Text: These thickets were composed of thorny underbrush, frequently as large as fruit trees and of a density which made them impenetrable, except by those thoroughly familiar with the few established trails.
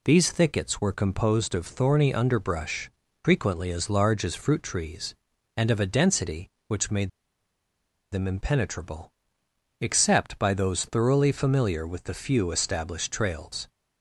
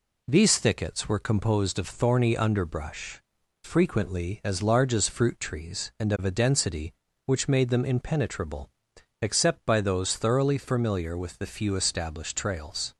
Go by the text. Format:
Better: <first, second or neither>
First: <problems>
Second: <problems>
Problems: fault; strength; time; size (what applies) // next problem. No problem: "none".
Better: second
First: pauses between "made" and "them"; at 7.0 s; 1.0 s long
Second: none